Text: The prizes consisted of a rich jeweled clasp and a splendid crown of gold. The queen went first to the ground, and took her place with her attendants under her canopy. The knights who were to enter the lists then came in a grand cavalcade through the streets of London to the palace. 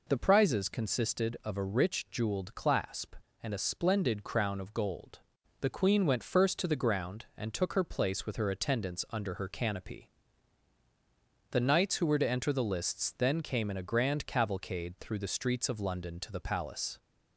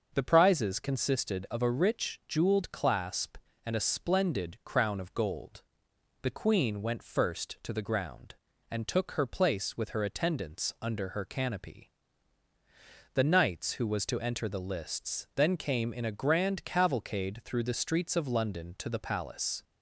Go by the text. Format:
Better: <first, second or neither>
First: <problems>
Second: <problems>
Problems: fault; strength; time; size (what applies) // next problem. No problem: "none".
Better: first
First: none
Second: starts louder than the rest; until 1.1 s; 6.5 dB // says "was" for "were"; at 13.8 s